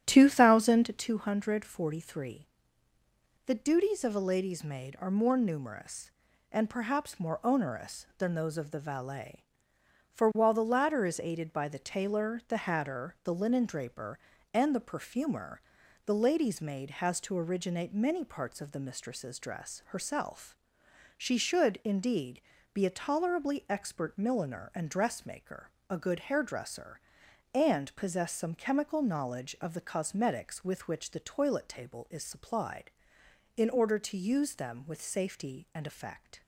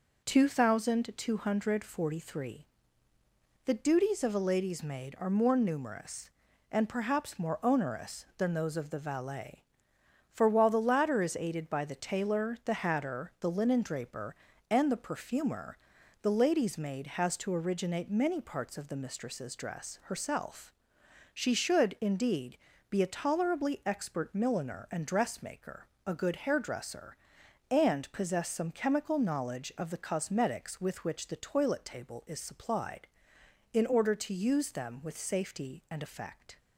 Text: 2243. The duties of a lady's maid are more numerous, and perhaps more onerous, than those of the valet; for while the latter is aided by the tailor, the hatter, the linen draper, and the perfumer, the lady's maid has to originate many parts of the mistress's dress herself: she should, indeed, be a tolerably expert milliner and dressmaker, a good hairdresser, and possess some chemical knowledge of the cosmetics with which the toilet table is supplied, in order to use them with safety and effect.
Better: second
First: starts louder than the rest; strong; until 1.2 s; 10.5 dB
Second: none

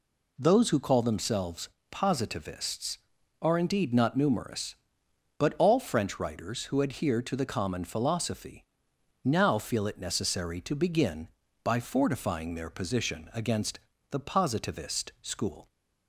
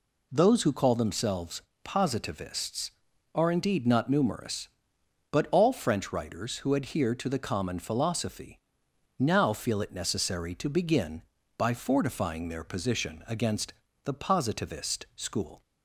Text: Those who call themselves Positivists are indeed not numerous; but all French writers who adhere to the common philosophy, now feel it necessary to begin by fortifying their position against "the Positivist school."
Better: neither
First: pauses between "themselves" and "Positivists"; slight; at 1.6 s; 0.24 s long // pauses between "against" and "the"; slight; at 13.7 s; 0.32 s long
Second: pauses between "themselves" and "Positivists"; slight; at 1.6 s; 0.24 s long // pauses between "against" and "the"; slight; at 13.7 s; 0.32 s long

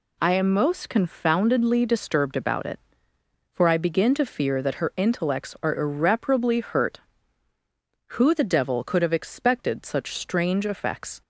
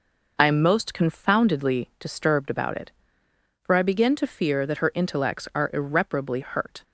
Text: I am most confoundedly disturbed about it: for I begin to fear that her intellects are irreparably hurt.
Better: second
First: goes on to say "Who the devil could have expected such strange effects"; strong; from 8.1 s on; 3.0 s long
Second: none

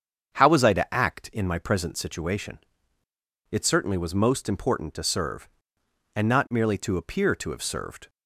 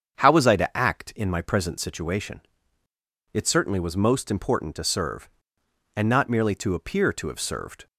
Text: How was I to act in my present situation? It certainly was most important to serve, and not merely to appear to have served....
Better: neither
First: starts louder than the rest; strong; until 1.3 s; 7.5 dB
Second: starts louder than the rest; strong; until 1.2 s; 7.5 dB

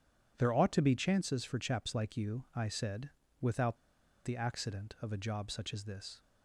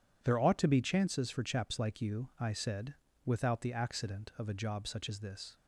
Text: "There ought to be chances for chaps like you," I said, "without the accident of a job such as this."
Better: second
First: pauses between "without" and "the"; noticeable; at 3.7 s; 0.48 s long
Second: none

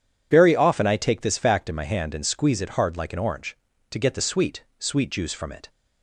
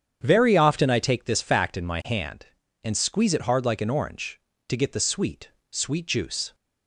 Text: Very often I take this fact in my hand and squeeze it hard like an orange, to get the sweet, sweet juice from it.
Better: first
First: none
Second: starts louder than the rest; strong; until 1.2 s; 8 dB // stops before "from it"; at 6.5 s

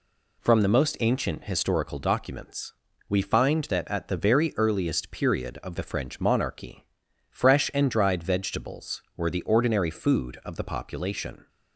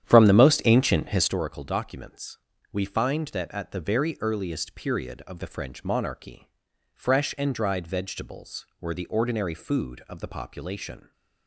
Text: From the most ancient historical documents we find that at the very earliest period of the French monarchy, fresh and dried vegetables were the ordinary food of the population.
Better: first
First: pauses between "documents" and "we"; slight; at 2.7 s; 0.34 s long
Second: starts louder than the rest; strong; until 1.4 s; 10 dB // pauses between "documents" and "we"; slight; at 2.3 s; 0.32 s long

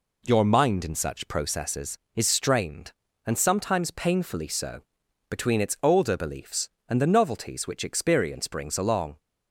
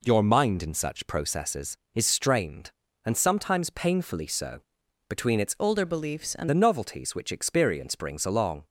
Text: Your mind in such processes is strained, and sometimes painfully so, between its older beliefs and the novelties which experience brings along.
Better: first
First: none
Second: changes voice from "older" to "and"; from 5.5 to 6.4 s; 0.9 s long

